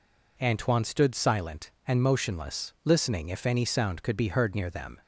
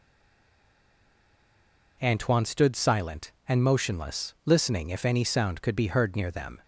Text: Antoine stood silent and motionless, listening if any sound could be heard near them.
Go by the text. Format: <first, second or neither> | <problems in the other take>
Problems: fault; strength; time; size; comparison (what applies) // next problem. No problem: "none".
first | stays silent before the first word; noticeable; until 1.9 s; 1.9 s long